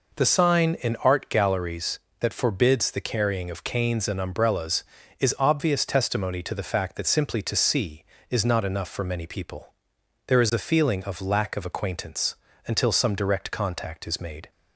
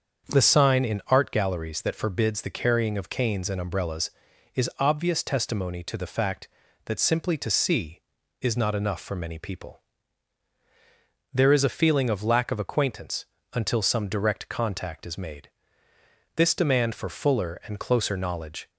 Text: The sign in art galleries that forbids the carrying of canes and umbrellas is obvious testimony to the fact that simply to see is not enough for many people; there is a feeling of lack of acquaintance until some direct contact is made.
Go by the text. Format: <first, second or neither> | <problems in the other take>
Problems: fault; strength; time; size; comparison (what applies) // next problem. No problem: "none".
first | starts louder than the rest; until 1.3 s; 7 dB // pauses between "acquaintance" and "until"; slight; at 13.2 s; 0.26 s long; slight in the first // goes on to say "This demand for fuller and closer knowledge"; strong; from 16.3 s on; 2.3 s long